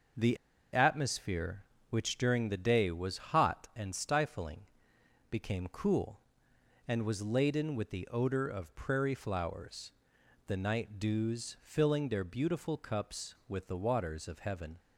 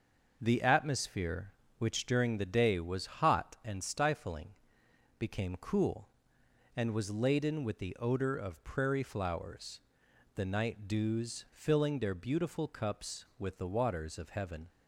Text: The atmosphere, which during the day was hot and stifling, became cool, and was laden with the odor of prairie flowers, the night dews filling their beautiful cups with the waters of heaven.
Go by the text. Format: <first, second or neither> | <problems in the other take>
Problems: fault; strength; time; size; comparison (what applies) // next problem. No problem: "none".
second | pauses between "The" and "atmosphere"; at 0.3 s; 0.37 s long